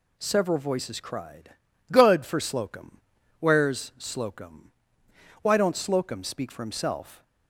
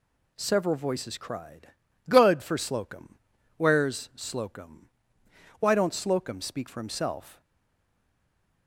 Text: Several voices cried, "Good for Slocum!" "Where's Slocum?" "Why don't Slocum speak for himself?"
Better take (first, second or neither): first